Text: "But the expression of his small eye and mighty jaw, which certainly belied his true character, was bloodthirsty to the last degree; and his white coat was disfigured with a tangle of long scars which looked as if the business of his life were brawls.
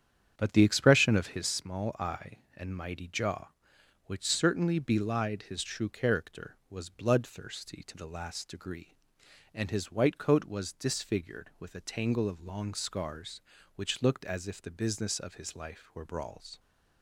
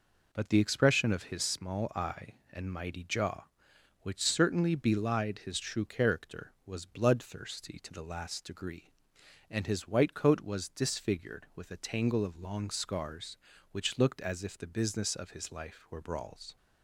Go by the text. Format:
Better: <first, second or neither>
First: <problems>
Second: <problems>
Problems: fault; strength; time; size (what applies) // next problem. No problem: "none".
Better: second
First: starts louder than the rest; strong; until 1.5 s; 8.5 dB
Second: none